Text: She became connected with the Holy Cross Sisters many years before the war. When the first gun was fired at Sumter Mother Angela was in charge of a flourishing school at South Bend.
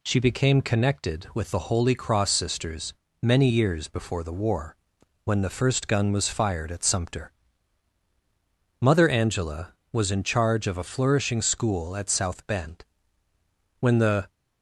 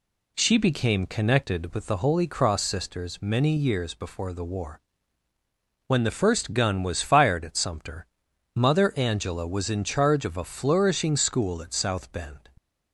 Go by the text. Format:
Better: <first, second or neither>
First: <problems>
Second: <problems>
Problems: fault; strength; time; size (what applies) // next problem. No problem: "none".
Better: second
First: pauses between "Sisters" and "many"; slight; at 2.9 s; 0.28 s long // pauses between "Sumter" and "Mother"; strong; at 7.3 s; 1.4 s long // goes on to say "When the"; from 13.7 s on; 0.50 s long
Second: pauses between "Sumter" and "Mother"; noticeable; at 8.0 s; 0.50 s long